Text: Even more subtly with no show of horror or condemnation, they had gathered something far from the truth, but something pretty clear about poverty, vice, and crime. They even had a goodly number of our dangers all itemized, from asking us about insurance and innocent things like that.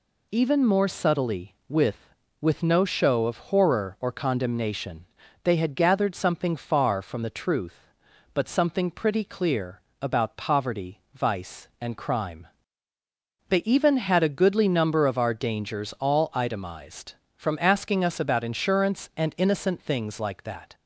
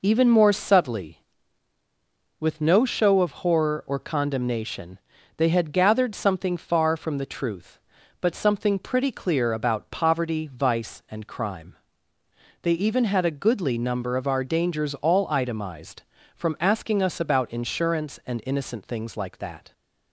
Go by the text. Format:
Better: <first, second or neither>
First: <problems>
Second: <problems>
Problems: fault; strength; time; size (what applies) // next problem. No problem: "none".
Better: second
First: says "with" twice; at 2.3 s // pauses between "clear" and "about"; slight; at 9.8 s; 0.20 s long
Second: none